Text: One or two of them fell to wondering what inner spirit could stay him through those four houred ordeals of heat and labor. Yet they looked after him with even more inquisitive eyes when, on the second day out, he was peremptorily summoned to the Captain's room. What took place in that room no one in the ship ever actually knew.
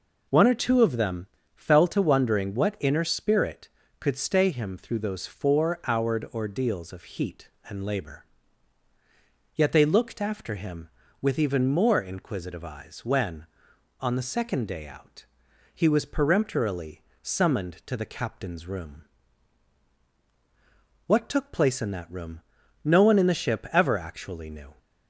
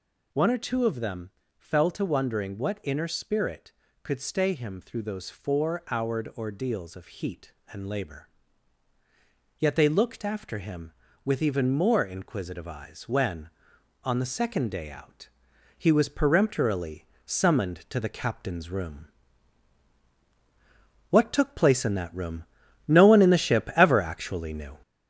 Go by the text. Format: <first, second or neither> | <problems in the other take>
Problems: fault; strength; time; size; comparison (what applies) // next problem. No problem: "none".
first | gets louder; noticeable; throughout; 4.5 dB // pauses between "them" and "fell"; slight; at 1.3 s; 0.28 s long; slight in the first // pauses between "peremptorily" and "summoned"; slight; at 17.0 s; 0.20 s long; slight in the first // pauses between "room" and "no"; at 22.4 s; 0.42 s long; also in the first